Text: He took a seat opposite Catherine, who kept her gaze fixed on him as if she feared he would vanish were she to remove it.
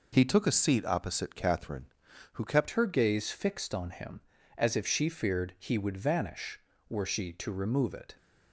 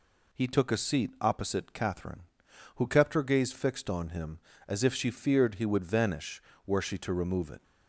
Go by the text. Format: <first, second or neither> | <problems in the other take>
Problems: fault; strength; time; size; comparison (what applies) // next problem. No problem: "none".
second | changes voice at "her"; from 2.7 s on; 5.4 s long